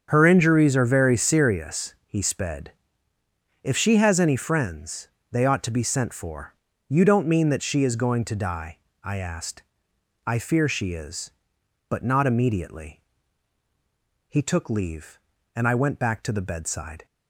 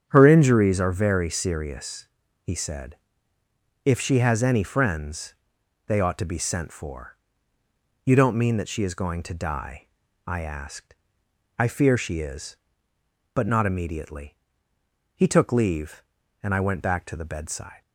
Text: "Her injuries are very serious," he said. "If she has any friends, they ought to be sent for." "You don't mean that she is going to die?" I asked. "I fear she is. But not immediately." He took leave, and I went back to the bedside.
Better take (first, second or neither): second